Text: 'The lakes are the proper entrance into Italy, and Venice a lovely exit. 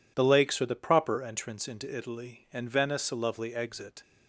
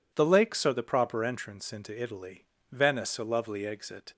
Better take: first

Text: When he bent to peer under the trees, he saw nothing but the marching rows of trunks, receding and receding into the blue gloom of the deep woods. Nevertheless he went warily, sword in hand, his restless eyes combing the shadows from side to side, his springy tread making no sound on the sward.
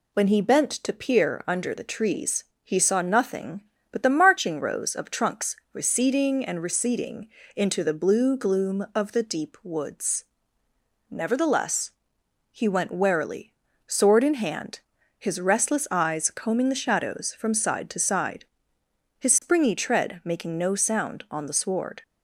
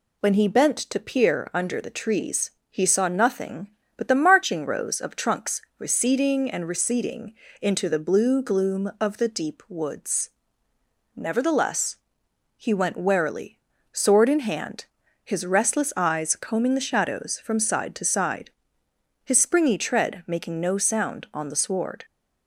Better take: neither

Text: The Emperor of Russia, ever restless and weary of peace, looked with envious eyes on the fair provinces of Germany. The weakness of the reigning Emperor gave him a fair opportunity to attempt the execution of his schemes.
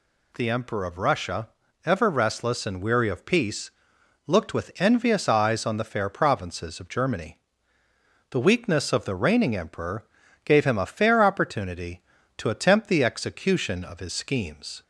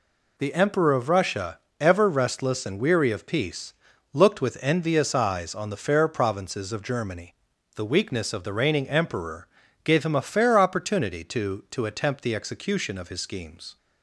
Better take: first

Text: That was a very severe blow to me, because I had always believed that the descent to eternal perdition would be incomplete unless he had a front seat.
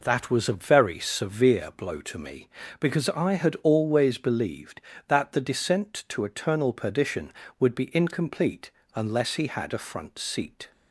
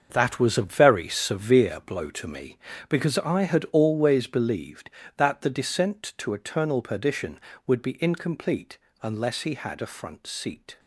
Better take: first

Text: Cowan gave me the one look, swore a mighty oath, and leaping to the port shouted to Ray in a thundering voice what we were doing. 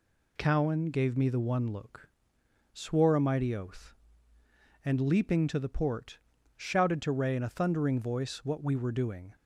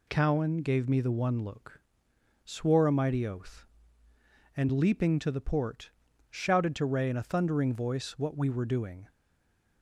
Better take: first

